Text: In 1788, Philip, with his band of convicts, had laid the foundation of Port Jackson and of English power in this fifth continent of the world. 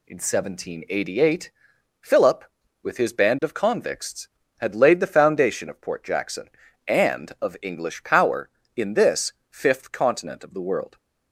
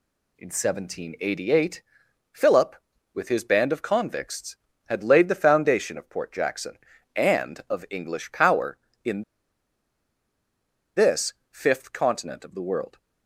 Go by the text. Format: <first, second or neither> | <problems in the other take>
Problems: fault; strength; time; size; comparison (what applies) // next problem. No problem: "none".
first | pauses between "in" and "this"; strong; at 9.2 s; 1.7 s long // pauses between "this" and "fifth"; slight; at 11.3 s; 0.16 s long; slight in the first